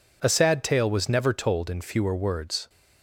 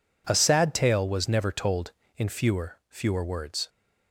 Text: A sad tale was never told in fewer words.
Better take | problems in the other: first | says "fewer" twice; at 2.8 s

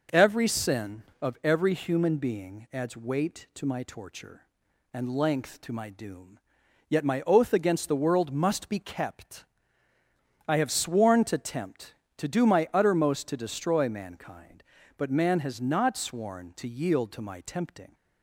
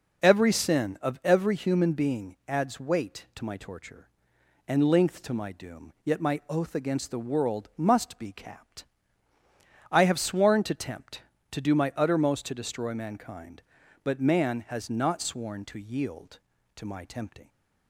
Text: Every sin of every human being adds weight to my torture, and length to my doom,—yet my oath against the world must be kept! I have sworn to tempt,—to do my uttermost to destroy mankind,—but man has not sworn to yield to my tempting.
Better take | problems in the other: first | says "capped" for "kept"; at 8.3 s

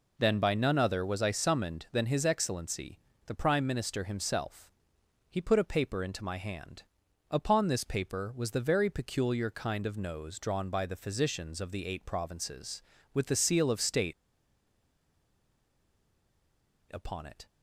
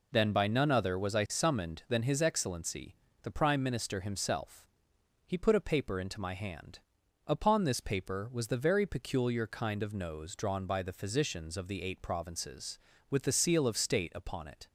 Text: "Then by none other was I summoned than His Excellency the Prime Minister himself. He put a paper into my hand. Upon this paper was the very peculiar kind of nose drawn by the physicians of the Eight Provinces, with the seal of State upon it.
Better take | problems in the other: second | pauses between "Excellency" and "the"; slight; at 3.0 s; 0.24 s long; slight in the second // pauses between "State" and "upon"; strong; at 14.1 s; 2.8 s long

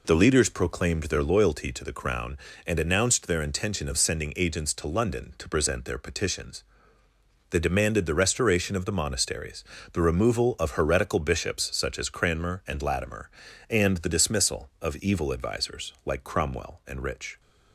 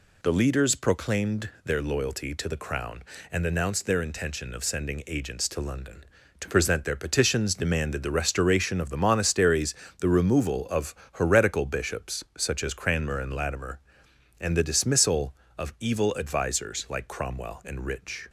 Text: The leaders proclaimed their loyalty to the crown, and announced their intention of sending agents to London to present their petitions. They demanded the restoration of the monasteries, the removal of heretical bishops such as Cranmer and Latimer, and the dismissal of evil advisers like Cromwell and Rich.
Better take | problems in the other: first | skips "They"; at 7.5 s // pauses between "of" and "heretical"; slight; at 10.9 s; 0.20 s long

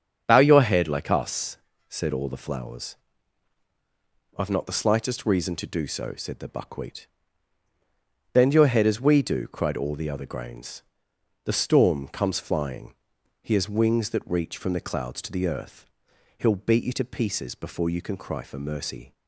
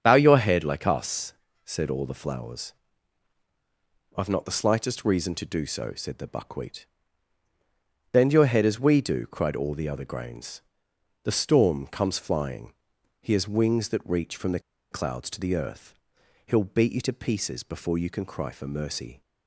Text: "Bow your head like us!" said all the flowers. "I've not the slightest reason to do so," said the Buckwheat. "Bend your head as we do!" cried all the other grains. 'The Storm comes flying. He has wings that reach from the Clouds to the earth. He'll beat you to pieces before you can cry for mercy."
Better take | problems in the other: first | starts louder than the rest; strong; until 1.0 s; 7.5 dB; strong in the first // pauses between "the" and "Clouds"; slight; at 14.5 s; 0.32 s long

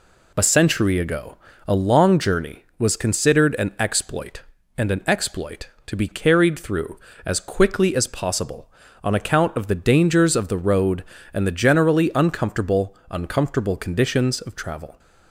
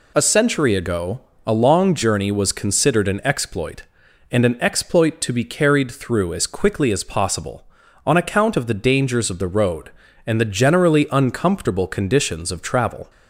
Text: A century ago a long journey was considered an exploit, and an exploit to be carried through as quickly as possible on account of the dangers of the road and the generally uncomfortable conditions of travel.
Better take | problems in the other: second | pauses between "ago" and "a"; slight; at 1.3 s; 0.30 s long; slight in the second // says "uncomfortable" twice; at 13.0 s

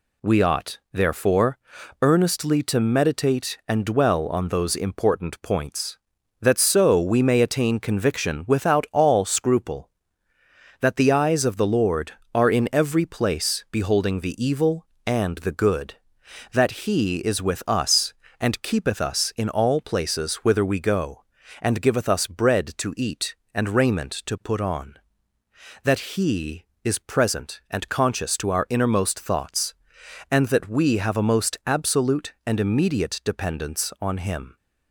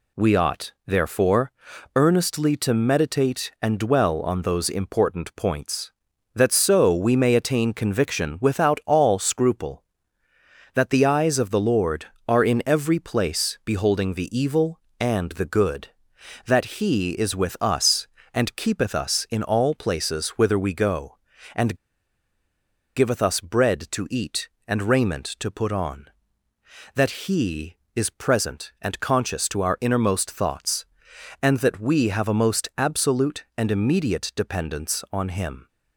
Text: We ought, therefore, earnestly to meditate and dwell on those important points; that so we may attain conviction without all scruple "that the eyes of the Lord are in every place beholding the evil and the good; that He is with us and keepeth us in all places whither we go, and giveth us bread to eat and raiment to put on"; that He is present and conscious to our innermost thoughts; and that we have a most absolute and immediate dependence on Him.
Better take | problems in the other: first | pauses between "and" and "giveth"; at 21.7 s; 1.2 s long

